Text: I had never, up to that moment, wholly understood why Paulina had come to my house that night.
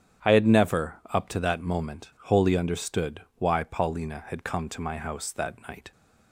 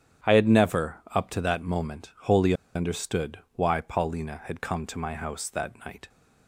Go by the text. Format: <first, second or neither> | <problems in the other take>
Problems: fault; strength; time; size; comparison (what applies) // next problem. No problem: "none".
first | starts louder than the rest; strong; until 1.4 s; 9 dB; strong in the first // pauses between "wholly" and "understood"; slight; at 2.5 s; 0.22 s long // pauses between "understood" and "why"; slight; at 3.4 s; 0.16 s long; slight in the first